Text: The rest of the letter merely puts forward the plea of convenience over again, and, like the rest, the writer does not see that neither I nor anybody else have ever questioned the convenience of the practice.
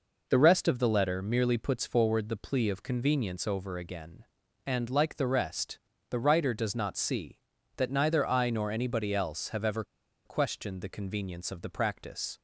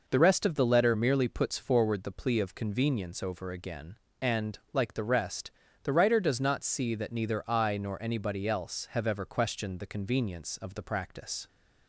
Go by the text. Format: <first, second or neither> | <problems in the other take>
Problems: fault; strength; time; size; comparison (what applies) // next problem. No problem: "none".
second | pauses between "ever" and "questioned"; at 9.8 s; 0.41 s long